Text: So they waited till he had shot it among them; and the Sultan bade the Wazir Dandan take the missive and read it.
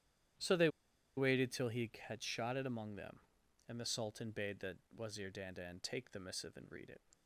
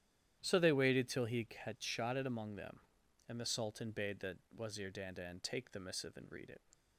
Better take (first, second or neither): second